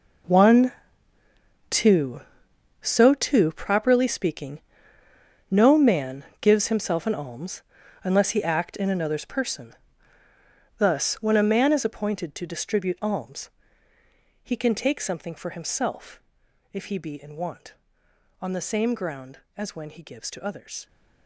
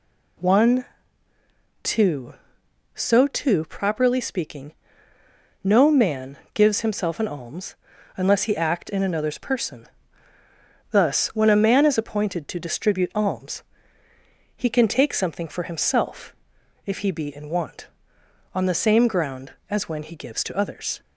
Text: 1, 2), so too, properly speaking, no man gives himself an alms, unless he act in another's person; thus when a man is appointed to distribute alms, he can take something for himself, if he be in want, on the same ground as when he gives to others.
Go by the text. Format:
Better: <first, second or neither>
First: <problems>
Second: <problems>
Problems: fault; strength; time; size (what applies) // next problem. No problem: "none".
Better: second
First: gets quieter; strong; throughout; 14 dB // pauses between "man" and "gives"; slight; at 6.2 s; 0.18 s long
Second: pauses between "man" and "gives"; slight; at 6.3 s; 0.18 s long